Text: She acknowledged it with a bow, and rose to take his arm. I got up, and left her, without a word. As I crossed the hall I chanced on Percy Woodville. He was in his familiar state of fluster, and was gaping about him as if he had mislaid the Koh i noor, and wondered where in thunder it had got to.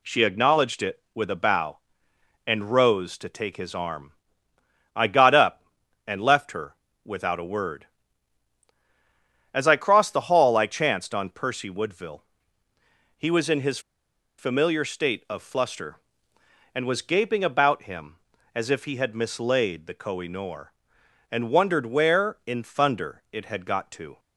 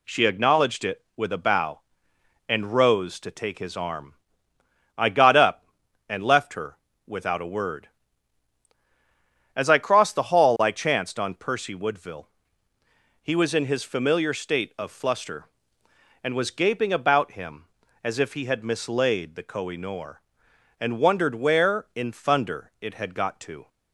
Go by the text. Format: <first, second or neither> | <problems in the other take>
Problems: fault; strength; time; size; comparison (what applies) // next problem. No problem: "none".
second | pauses between "his" and "familiar"; noticeable; at 13.7 s; 0.59 s long